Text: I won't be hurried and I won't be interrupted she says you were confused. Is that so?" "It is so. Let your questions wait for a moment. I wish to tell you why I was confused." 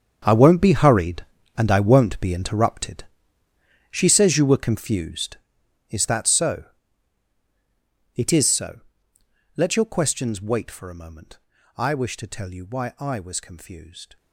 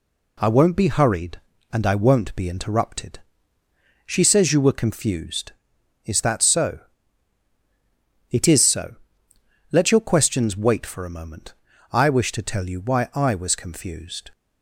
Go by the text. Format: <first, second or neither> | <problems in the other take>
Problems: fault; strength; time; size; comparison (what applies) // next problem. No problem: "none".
second | gets quieter; strong; throughout; 15 dB // pauses between "interrupted" and "she"; noticeable; at 3.0 s; 0.88 s long; noticeable in the second